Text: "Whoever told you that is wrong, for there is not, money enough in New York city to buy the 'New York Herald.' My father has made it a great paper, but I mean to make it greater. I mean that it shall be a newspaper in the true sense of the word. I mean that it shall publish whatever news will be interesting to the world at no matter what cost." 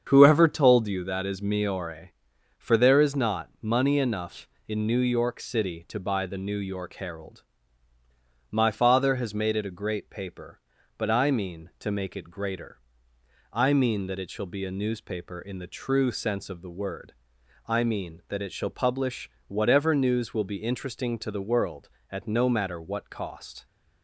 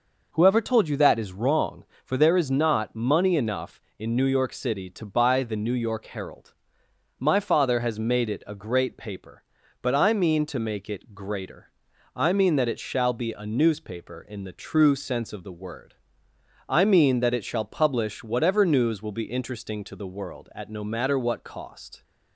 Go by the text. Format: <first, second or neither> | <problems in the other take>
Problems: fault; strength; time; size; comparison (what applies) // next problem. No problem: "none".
second | starts louder than the rest; strong; until 1.0 s; 7.5 dB // says "miore" for "wrong"; at 1.4 s // pauses between "publish" and "whatever"; slight; at 19.2 s; 0.18 s long